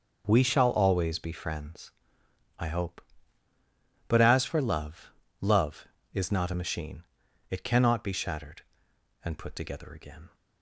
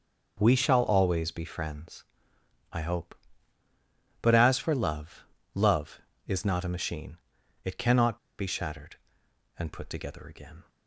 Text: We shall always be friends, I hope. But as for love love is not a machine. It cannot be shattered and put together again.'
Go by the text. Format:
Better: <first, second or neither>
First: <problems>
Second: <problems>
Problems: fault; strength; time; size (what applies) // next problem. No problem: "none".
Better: first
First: pauses between "love" and "love"; slight; at 5.1 s; 0.30 s long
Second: pauses between "love" and "love"; slight; at 5.2 s; 0.30 s long // pauses between "cannot" and "be"; slight; at 8.1 s; 0.22 s long